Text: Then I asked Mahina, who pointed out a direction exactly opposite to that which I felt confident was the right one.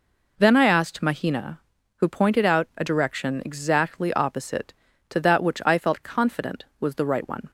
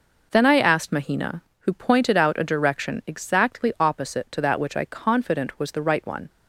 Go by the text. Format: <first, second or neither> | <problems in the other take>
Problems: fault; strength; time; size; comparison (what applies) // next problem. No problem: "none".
first | skips "felt"; at 4.8 s